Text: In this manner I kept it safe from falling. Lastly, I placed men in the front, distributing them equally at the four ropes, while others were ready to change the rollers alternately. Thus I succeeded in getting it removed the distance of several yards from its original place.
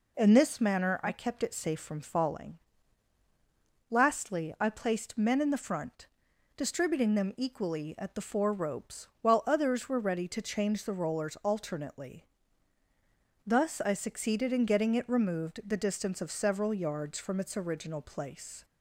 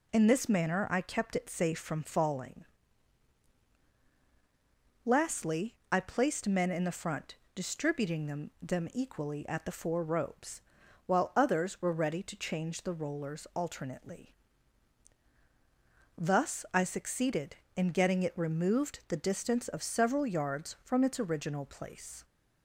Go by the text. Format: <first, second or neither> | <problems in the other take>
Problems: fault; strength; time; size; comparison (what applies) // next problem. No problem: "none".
first | says "them" twice; at 8.6 s